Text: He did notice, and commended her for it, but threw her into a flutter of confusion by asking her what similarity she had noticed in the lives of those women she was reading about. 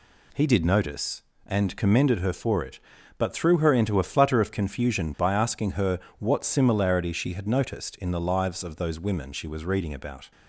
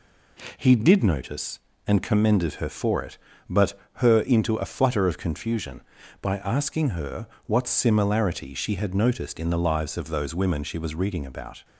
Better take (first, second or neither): first